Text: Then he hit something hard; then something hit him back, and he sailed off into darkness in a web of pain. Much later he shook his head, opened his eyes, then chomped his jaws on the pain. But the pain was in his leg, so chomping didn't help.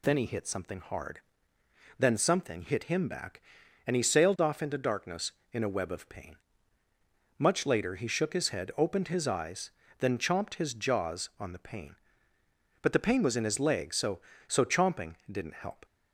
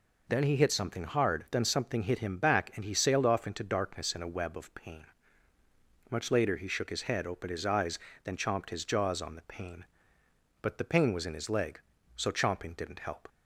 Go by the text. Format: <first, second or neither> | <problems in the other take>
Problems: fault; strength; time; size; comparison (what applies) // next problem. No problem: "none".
second | says "so" twice; at 14.4 s